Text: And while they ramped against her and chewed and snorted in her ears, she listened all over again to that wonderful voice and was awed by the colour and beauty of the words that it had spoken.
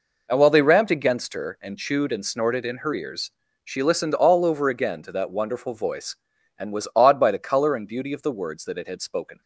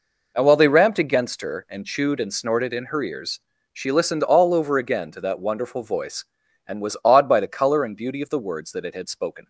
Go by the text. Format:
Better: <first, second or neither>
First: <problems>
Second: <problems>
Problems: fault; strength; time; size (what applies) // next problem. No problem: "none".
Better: neither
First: none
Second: none